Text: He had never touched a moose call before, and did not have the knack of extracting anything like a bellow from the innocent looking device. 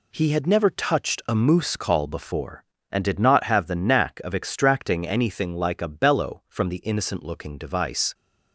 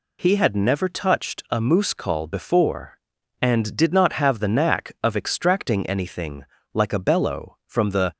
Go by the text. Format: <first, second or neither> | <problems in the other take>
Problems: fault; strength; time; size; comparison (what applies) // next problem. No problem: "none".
first | pauses between "anything" and "like"; slight; at 6.4 s; 0.30 s long // stops before "innocent looking device"; at 8.1 s